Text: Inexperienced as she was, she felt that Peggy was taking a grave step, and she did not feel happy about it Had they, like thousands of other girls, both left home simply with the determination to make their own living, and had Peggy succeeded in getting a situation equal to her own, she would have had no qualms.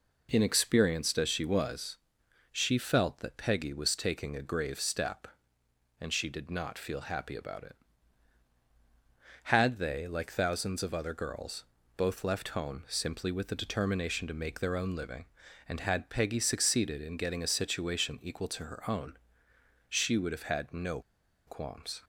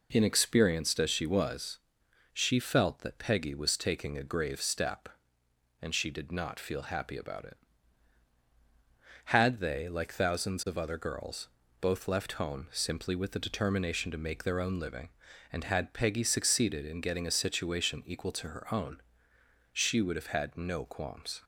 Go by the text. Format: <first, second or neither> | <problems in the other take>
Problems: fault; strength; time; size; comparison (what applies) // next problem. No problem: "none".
second | pauses between "no" and "qualms"; noticeable; at 20.9 s; 0.47 s long